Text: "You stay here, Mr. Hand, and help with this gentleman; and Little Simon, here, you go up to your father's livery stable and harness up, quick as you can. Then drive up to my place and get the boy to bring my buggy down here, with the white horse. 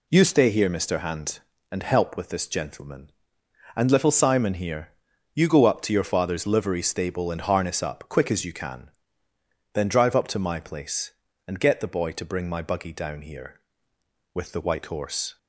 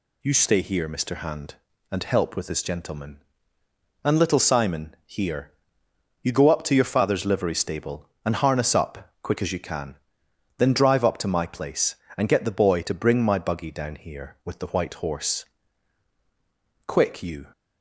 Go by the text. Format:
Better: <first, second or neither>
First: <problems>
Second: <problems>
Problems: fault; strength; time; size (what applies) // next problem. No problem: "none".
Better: first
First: none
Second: goes on to say "Quick you"; noticeable; from 16.8 s on; 0.64 s long